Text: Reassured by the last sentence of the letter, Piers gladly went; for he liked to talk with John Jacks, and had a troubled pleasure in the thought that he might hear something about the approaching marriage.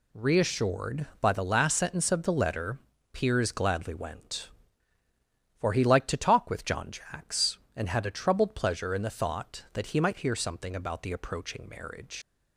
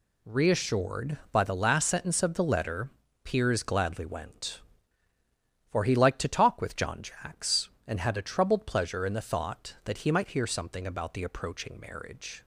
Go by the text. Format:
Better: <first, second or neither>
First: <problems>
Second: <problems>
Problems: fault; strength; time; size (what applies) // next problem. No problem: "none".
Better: second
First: leaves "marriage" unfinished; at 12.2 s; 115 ms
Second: none